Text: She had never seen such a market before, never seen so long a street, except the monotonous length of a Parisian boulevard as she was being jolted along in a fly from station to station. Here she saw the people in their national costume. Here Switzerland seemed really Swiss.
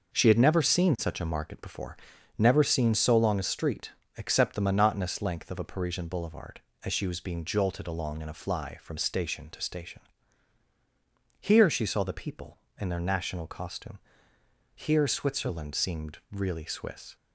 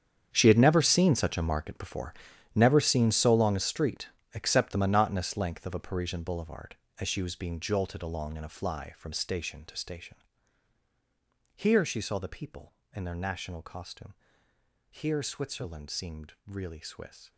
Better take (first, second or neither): first